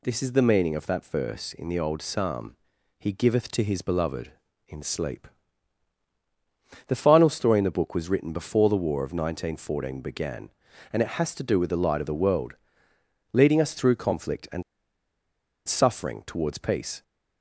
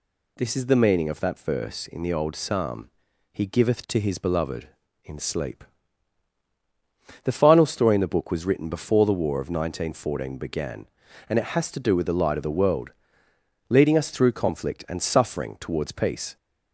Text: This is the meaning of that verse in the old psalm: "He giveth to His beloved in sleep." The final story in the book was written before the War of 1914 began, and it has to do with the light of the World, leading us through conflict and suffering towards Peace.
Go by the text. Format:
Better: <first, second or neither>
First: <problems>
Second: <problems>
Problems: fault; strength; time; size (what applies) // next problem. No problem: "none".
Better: second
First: pauses between "and" and "suffering"; at 14.6 s; 1.0 s long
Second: none